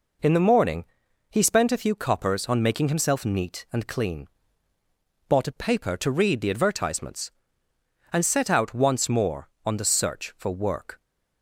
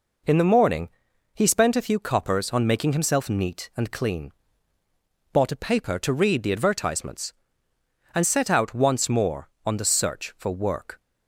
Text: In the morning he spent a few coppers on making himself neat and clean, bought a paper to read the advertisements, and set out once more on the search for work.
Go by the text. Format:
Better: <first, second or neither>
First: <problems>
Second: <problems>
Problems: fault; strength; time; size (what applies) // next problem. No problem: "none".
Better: neither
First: pauses between "morning" and "he"; noticeable; at 0.8 s; 0.46 s long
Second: pauses between "morning" and "he"; noticeable; at 0.8 s; 0.46 s long